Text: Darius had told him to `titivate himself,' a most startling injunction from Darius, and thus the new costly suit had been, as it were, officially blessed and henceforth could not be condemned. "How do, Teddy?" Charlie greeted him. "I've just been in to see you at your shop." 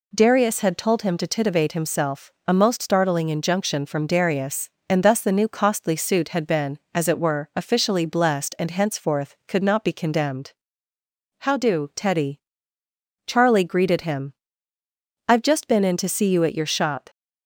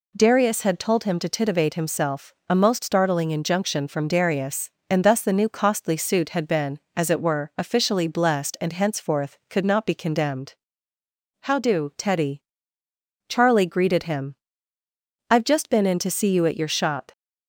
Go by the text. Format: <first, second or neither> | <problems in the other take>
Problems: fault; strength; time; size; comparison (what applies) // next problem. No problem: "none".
neither | none